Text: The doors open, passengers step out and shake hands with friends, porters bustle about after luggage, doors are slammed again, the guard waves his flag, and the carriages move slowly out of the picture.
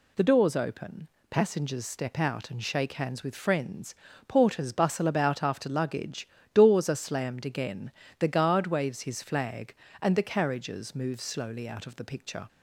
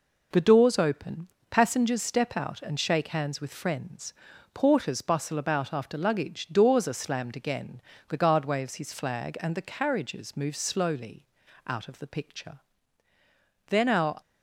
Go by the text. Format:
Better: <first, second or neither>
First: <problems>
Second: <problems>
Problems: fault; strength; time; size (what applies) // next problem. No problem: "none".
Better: first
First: none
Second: pauses between "slowly" and "out"; at 11.2 s; 0.42 s long // goes on to say "Then our"; from 13.6 s on; 0.54 s long